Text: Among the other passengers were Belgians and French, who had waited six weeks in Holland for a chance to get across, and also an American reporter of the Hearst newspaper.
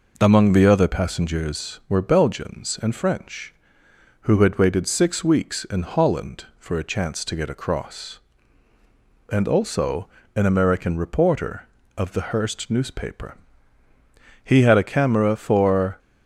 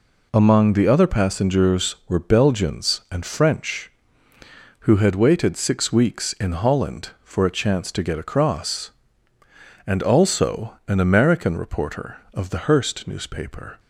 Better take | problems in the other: second | pauses between "also" and "an"; slight; at 10.0 s; 0.28 s long // goes on to say "He had a camera for"; from 14.4 s on; 1.5 s long

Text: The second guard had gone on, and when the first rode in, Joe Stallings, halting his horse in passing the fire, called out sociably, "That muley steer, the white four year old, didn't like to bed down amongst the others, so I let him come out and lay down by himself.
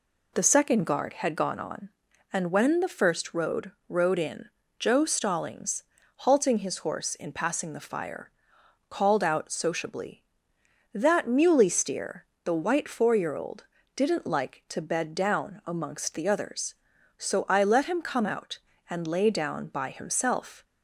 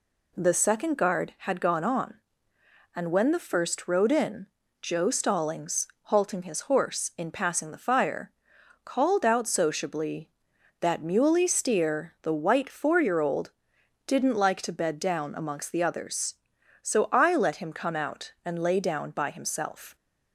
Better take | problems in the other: second | says "rode" twice; at 3.8 s

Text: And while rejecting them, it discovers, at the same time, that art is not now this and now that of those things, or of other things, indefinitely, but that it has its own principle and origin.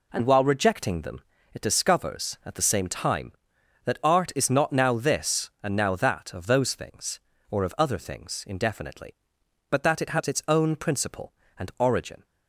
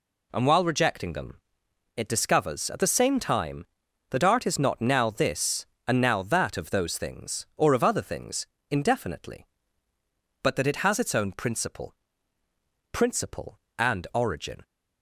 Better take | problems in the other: first | says "principle" twice; at 12.9 s

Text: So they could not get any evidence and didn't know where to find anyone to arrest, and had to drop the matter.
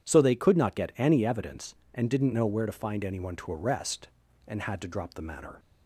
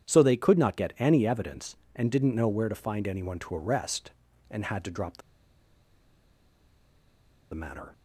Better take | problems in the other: first | pauses between "the" and "matter"; strong; at 5.2 s; 2.3 s long

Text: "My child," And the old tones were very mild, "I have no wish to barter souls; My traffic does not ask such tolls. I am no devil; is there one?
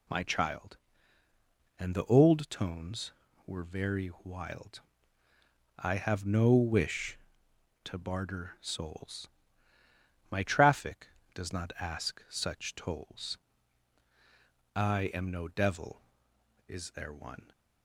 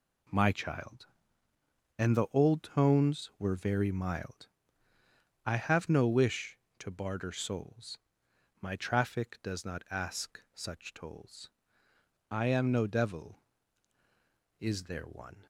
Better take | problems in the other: second | says "wild" for "mild"; at 4.2 s

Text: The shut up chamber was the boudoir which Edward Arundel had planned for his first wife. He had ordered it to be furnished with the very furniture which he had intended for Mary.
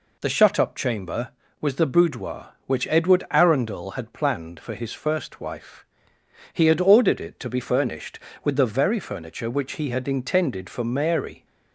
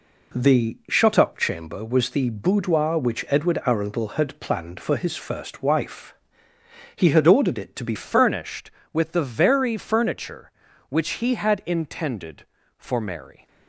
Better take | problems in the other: first | changes voice at "furnished"; from 7.9 s on; 5.5 s long

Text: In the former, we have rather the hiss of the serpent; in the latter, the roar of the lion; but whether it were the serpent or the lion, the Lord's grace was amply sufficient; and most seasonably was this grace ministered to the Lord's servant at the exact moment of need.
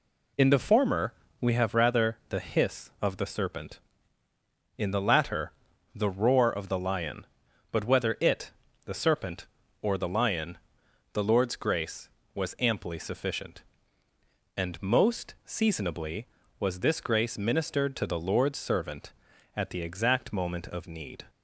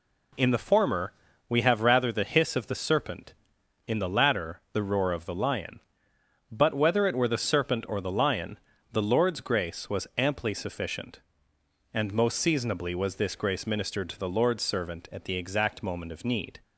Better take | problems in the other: second | skips "were"; at 8.6 s

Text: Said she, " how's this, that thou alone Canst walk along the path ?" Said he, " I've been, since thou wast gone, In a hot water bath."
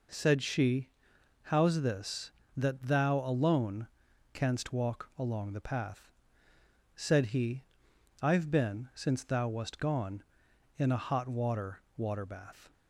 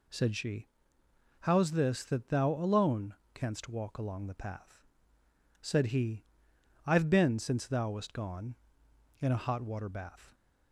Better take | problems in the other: second | pauses between "alone" and "Canst"; noticeable; at 3.8 s; 0.48 s long; slight in the second // says "water" twice; at 11.9 s

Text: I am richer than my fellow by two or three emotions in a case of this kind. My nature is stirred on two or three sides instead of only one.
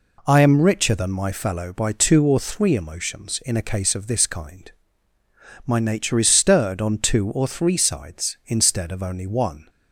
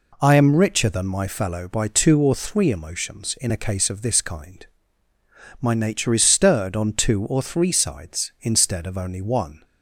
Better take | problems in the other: neither | none

